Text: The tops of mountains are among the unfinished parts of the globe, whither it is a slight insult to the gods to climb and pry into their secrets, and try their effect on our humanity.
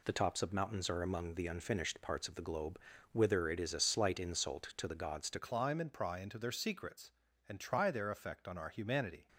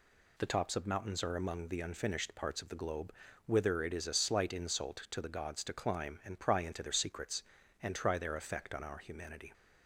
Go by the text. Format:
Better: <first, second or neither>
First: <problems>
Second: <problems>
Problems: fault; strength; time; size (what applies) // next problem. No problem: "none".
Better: second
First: changes voice at "climb"; from 5.3 s on; 3.9 s long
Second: none